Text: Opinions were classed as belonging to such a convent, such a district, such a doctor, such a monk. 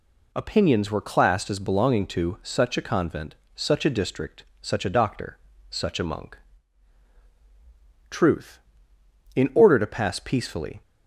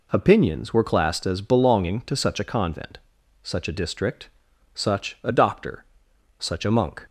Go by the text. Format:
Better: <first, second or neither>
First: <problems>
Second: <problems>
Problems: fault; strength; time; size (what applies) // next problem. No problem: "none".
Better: second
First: goes on to say "Truth in order to pass peacefully"; strong; from 8.0 s on; 2.7 s long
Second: none